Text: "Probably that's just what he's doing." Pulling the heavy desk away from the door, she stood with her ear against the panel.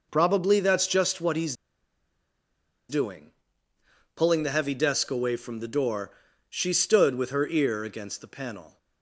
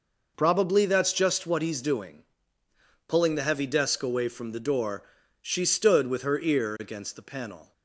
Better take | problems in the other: second | pauses between "he's" and "doing"; strong; at 1.5 s; 1.3 s long

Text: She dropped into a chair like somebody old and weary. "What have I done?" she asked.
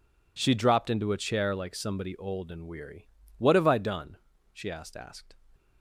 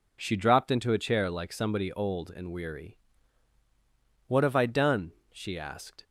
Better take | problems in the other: second | says "asked" twice; at 4.9 s

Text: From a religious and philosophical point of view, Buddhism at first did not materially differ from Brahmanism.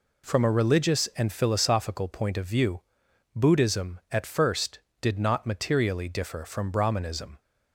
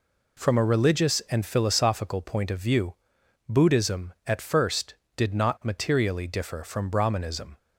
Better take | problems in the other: neither | none

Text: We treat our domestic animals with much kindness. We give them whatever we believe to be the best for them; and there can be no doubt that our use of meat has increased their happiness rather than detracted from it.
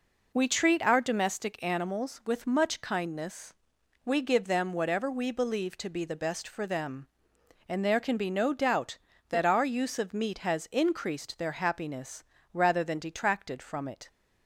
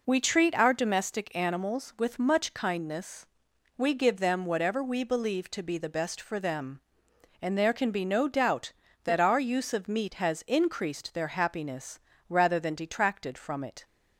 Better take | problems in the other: neither | pauses between "happiness" and "rather"; slight; the same in both

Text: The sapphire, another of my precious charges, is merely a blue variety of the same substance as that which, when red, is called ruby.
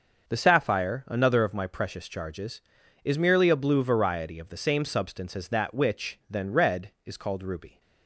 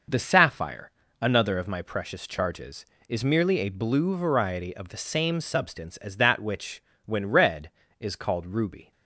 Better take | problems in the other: second | starts louder than the rest; until 1.3 s; 6.5 dB // says "then" for "when"; at 6.2 s

